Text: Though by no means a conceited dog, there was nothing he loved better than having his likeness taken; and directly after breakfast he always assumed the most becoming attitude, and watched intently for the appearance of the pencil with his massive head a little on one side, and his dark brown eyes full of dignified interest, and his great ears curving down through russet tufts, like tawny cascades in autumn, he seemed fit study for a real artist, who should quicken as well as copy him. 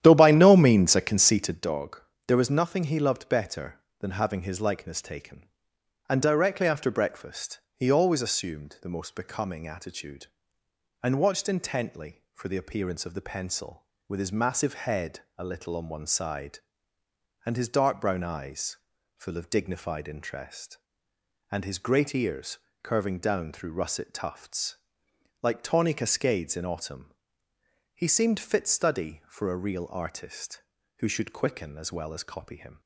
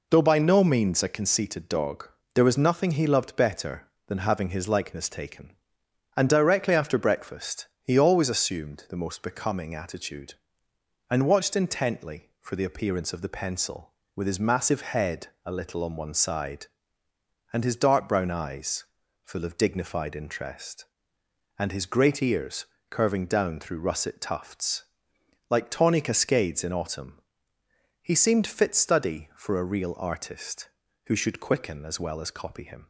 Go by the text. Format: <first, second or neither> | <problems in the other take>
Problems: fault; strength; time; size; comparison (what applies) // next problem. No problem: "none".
second | starts louder than the rest; strong; until 1.7 s; 11 dB // pauses between "breakfast" and "he"; slight; at 7.6 s; 0.16 s long; slight in the second // pauses between "head" and "a"; slight; at 15.2 s; 0.16 s long; slight in the second // pauses between "eyes" and "full"; at 18.7 s; 0.38 s long; also in the second // pauses between "ears" and "curving"; slight; at 22.5 s; 0.26 s long; slight in the second